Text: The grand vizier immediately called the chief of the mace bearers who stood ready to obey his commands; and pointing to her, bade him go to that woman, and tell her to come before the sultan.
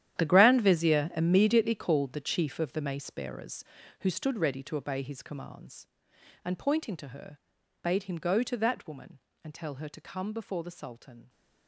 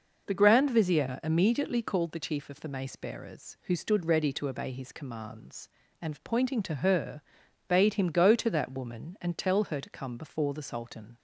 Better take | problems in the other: second | gets quieter; strong; throughout; 14.5 dB

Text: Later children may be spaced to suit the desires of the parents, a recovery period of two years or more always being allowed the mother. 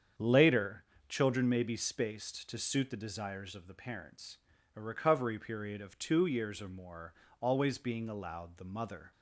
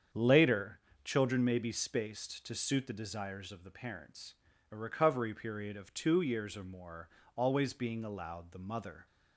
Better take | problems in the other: neither | starts louder than the rest; strong; the same in both // pauses between "Later" and "children"; slight; the same in both // pauses between "more" and "always"; slight; the same in both

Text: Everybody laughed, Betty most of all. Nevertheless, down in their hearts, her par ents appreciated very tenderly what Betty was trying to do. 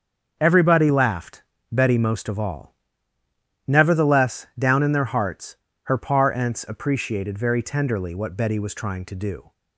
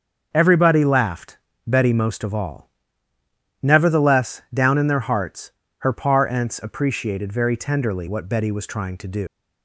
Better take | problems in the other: first | starts louder than the rest; until 1.3 s; 6.5 dB; also in the first // leaves "do" unfinished; at 9.2 s; 175 ms

